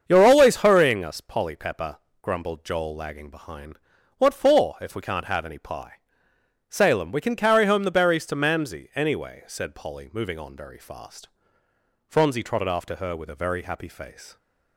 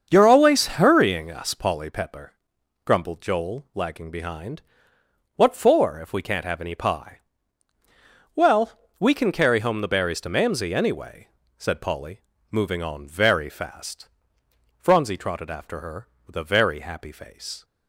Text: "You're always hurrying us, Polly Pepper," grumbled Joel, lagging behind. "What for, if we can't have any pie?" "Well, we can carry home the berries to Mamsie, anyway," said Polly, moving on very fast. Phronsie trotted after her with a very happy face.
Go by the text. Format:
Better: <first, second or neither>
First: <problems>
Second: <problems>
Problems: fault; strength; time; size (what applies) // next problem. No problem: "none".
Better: second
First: starts louder than the rest; until 1.0 s; 7 dB // says "Salem" for "Well"; at 6.6 s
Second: starts louder than the rest; until 1.1 s; 7 dB